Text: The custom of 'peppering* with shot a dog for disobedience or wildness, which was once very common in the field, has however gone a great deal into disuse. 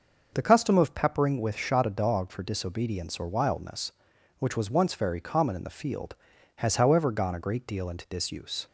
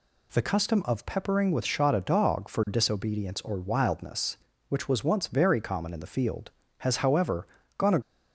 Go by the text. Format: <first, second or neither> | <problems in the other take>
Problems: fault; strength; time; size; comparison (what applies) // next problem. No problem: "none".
first | pauses between "however" and "gone"; slight; at 7.4 s; 0.32 s long // stops before "great deal into disuse"; at 8.0 s